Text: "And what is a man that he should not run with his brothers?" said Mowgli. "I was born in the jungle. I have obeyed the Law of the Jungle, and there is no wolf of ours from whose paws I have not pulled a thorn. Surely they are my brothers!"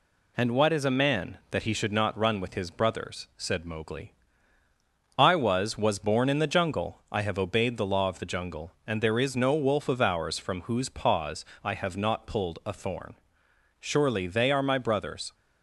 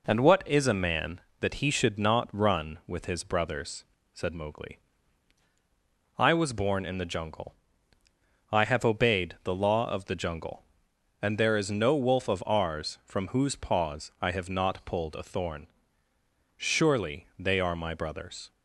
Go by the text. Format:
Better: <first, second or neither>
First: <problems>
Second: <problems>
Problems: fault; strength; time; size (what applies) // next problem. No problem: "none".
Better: second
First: says "was" twice; at 5.7 s // pauses between "paws" and "I"; slight; at 11.4 s; 0.18 s long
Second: none